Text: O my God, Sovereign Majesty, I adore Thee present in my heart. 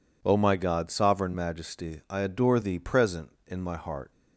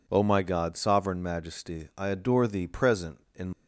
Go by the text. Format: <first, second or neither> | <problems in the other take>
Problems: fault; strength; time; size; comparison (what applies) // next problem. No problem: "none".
first | stops before "my heart"; at 3.5 s